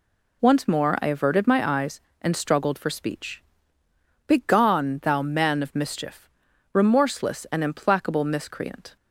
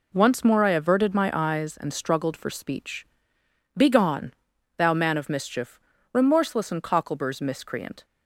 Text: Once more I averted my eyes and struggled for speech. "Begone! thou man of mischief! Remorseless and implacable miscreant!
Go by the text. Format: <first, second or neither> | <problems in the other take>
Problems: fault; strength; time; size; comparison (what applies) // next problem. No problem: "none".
first | says "cockleburs" for "implacable"; at 6.8 s